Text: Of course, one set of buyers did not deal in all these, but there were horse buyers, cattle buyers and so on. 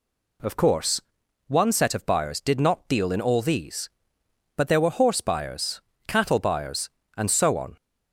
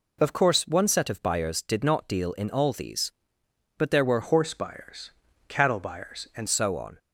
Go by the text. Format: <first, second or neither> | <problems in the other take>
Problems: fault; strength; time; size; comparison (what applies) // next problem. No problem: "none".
first | changes voice from "horse" to "and"; from 4.2 to 6.4 s; 2.2 s long